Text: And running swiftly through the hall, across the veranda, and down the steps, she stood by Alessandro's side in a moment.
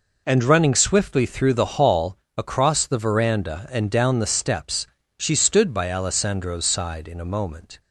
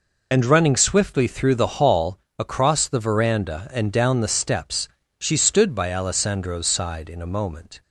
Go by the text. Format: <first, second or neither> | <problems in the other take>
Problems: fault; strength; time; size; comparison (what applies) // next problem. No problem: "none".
first | loses the start of "And"; at 0.3 s; 35 ms